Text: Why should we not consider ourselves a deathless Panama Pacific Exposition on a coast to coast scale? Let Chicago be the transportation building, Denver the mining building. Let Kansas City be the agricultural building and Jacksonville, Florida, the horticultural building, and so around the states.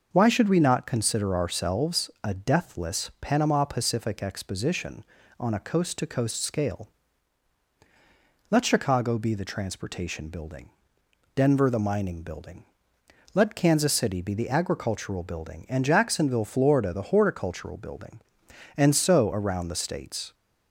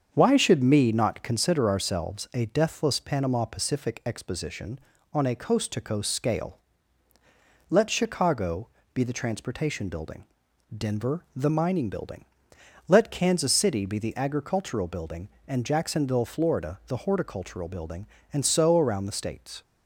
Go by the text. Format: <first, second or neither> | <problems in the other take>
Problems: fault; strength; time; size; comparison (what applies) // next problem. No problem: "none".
first | starts louder than the rest; until 1.1 s; 7 dB; noticeable in the first // says "me" for "we"; at 0.6 s // pauses between "Chicago" and "be"; slight; at 8.6 s; 0.26 s long